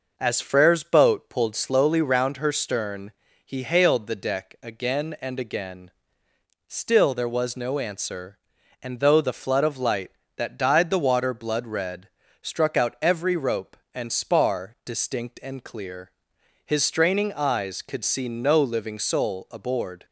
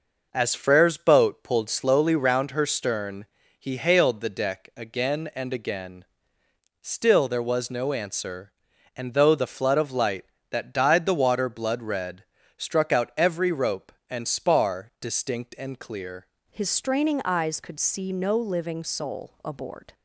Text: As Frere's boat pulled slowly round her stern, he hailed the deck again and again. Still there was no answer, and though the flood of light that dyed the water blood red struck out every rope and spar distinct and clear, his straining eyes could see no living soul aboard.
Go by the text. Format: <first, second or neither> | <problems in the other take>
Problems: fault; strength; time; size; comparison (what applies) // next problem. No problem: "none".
first | pauses between "red" and "struck"; slight; at 12.2 s; 0.34 s long; slight in the first // changes voice at "his"; from 16.5 s on; 3.4 s long